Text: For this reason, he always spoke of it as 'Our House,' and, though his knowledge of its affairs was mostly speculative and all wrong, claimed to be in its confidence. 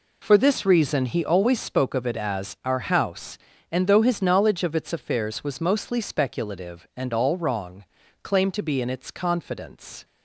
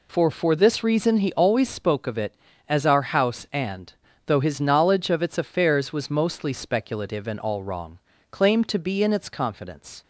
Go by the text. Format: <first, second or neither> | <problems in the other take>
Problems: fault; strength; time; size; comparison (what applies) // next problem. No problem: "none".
first | says "For" twice; at 0.2 s